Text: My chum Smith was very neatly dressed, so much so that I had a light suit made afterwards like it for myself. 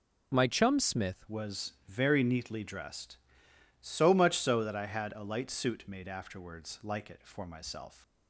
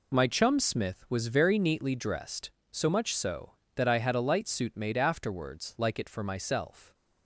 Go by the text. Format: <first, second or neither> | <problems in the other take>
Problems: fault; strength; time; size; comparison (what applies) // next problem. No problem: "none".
second | changes voice at "was"; from 1.2 s on; 6.8 s long